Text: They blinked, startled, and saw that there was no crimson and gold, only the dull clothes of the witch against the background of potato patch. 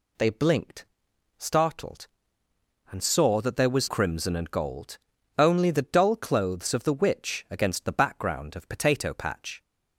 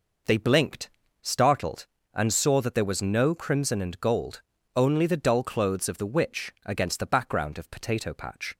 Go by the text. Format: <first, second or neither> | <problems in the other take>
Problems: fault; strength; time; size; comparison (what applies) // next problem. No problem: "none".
second | skips "no"; at 3.8 s